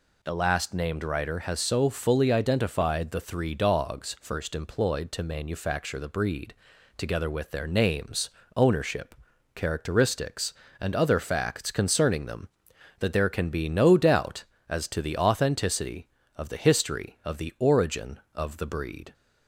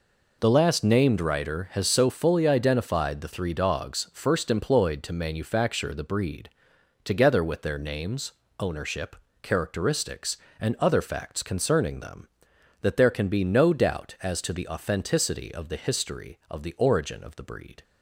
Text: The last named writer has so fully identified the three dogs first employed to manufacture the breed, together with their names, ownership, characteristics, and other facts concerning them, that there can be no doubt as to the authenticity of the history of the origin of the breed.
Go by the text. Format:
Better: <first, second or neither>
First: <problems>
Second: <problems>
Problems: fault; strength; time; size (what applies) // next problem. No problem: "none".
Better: neither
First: none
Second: none